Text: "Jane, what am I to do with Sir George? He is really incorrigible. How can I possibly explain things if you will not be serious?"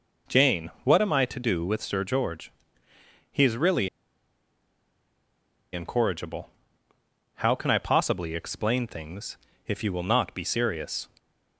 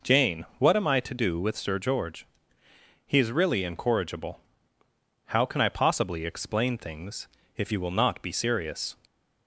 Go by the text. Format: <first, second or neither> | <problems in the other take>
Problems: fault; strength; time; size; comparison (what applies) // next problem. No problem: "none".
second | pauses between "really" and "incorrigible"; strong; at 3.8 s; 1.8 s long // pauses between "things" and "if"; slight; at 9.3 s; 0.30 s long; slight in the second